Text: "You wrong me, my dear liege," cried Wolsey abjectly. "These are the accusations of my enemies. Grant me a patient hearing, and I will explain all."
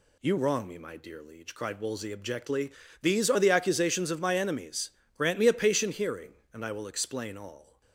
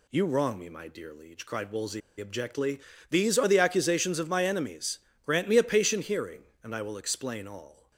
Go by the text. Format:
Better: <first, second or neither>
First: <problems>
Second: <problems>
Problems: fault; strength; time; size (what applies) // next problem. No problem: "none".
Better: first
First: none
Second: pauses between "Wolsey" and "abjectly"; slight; at 2.0 s; 0.18 s long